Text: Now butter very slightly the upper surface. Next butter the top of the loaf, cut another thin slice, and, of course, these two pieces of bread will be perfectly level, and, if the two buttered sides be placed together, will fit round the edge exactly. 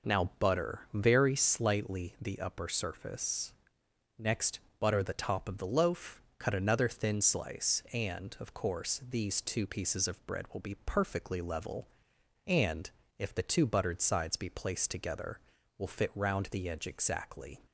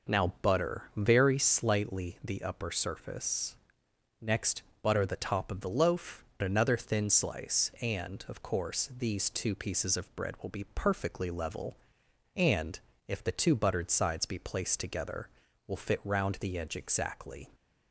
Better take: first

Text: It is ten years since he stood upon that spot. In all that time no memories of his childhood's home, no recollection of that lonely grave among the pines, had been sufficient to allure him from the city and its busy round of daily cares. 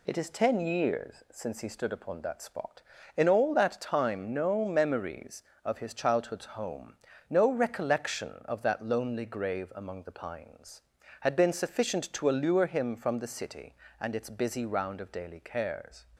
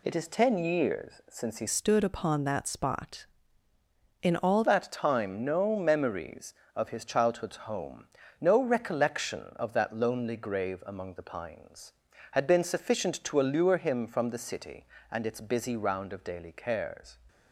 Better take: first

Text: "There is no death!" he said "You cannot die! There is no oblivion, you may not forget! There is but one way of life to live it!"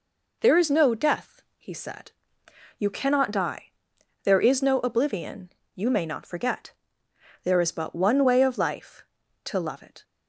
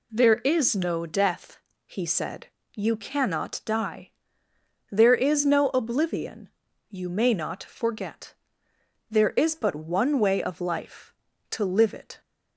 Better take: second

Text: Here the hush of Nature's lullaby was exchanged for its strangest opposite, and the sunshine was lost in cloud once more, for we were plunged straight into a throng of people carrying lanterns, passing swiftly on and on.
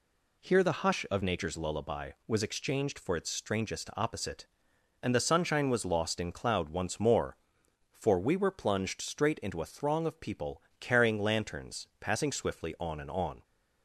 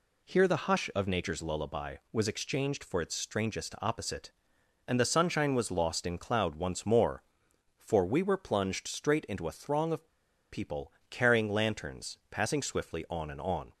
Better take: first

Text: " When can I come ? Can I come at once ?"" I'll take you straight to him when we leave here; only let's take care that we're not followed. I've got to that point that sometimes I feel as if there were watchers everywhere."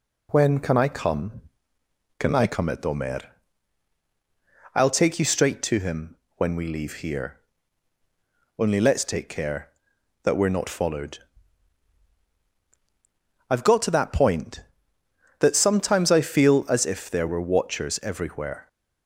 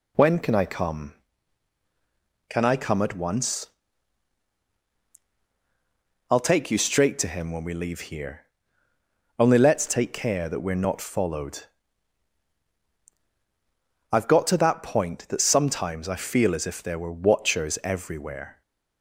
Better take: second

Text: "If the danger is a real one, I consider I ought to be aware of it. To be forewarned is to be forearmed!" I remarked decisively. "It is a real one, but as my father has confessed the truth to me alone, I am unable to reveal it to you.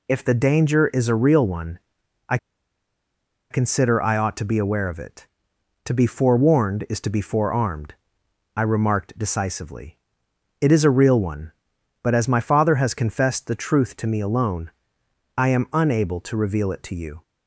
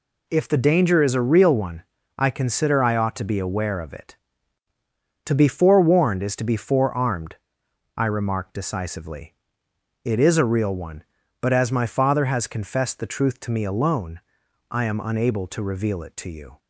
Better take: second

